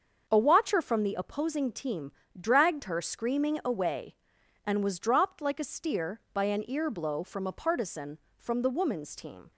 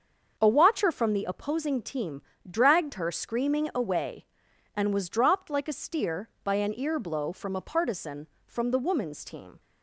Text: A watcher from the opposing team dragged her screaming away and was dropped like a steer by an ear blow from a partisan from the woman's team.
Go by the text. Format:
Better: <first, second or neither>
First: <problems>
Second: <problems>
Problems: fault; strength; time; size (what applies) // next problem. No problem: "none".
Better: neither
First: starts louder than the rest; until 1.2 s; 6.5 dB // pauses between "team" and "dragged"; slight; at 2.1 s; 0.28 s long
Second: starts louder than the rest; until 1.3 s; 6.5 dB // pauses between "team" and "dragged"; slight; at 2.2 s; 0.28 s long